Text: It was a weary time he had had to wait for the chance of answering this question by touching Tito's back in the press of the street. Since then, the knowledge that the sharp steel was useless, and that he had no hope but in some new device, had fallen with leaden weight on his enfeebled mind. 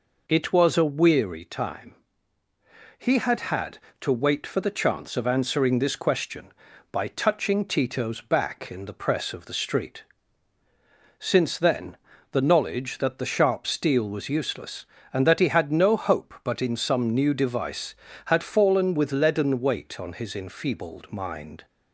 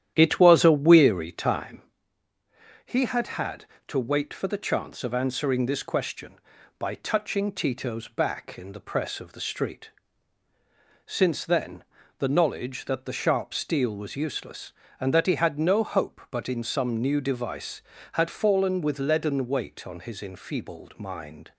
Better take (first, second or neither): first